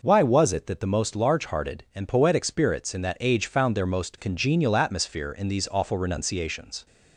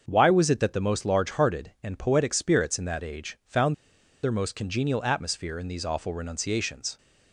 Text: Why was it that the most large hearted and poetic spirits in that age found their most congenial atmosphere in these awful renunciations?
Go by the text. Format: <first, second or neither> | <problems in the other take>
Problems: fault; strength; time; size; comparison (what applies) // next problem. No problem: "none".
first | starts louder than the rest; until 1.0 s; 6.5 dB // pauses between "found" and "their"; noticeable; at 3.7 s; 0.48 s long